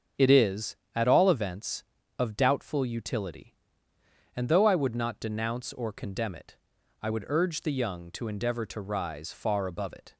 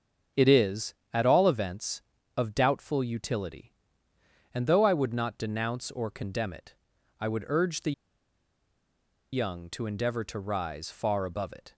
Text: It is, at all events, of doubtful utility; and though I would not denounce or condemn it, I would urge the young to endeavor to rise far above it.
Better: first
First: starts louder than the rest; strong; until 1.3 s; 7 dB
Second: starts louder than the rest; strong; until 1.5 s; 7 dB // pauses between "the" and "young"; strong; at 7.9 s; 1.4 s long

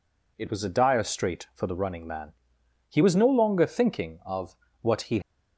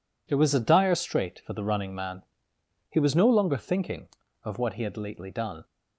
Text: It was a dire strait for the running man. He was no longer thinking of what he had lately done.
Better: second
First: pauses between "of" and "what"; slight; at 4.5 s; 0.24 s long // stops before "had lately done"; at 5.2 s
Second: none

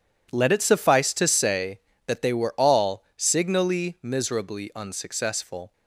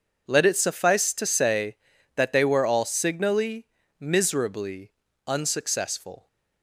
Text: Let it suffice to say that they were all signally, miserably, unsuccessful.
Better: neither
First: none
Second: none

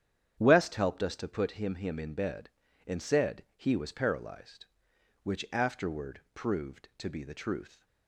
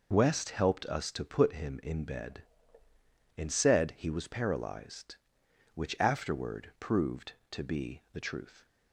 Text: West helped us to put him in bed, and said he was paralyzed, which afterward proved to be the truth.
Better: second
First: starts louder than the rest; strong; until 1.4 s; 9 dB // says "him" twice; at 1.7 s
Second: none

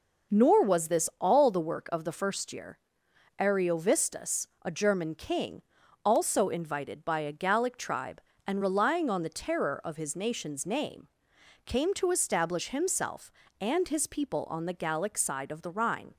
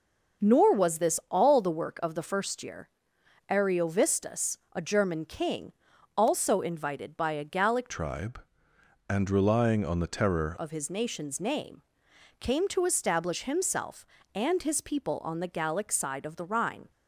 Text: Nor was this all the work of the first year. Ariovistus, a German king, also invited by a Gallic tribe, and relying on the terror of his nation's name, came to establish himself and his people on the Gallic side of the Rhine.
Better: first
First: none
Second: starts louder than the rest; until 1.5 s; 6.5 dB // changes voice from "tribe" to "terror"; from 7.8 to 10.5 s; 2.7 s long

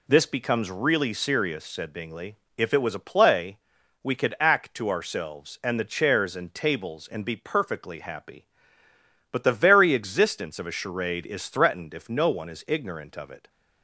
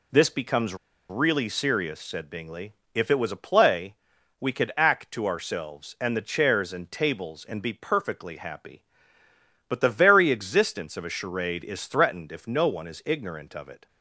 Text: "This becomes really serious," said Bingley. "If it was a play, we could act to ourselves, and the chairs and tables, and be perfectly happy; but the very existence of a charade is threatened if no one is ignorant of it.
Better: first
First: none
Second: pauses between "becomes" and "really"; slight; at 0.7 s; 0.34 s long

